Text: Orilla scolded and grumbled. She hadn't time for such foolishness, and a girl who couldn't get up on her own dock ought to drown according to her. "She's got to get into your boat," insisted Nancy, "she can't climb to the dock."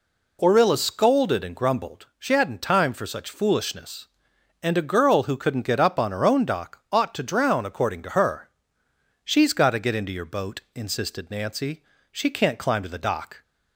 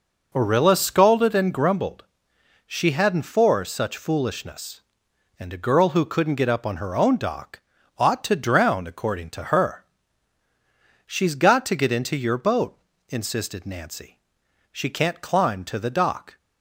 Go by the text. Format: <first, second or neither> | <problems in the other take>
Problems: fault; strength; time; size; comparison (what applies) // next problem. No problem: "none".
first | skips "time"; at 3.2 s // pauses between "dock" and "ought"; at 7.5 s; 0.40 s long